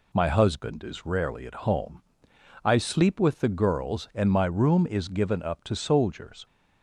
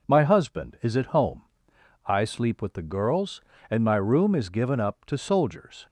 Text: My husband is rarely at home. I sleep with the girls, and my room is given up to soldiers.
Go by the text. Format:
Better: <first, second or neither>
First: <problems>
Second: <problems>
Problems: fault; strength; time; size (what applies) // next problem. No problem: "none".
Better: first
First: none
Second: skips "rarely"; at 0.9 s